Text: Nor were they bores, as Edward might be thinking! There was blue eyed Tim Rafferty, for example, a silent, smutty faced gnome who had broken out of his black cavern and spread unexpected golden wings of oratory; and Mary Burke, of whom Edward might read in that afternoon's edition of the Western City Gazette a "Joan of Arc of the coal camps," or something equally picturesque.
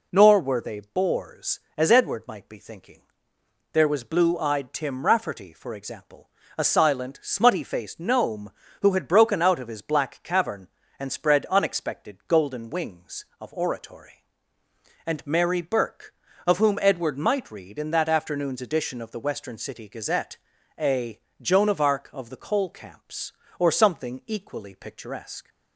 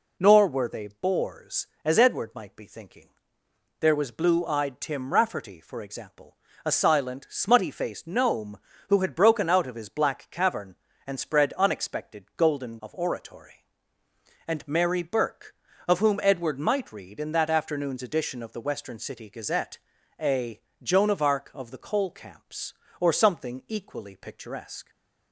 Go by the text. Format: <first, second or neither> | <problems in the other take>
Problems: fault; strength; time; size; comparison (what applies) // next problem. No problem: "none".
first | skips "wings"; at 12.8 s // pauses between "Gazette" and "a"; at 19.7 s; 0.42 s long; also in the first // pauses between "a" and "Joan"; slight; at 20.5 s; 0.22 s long; slight in the first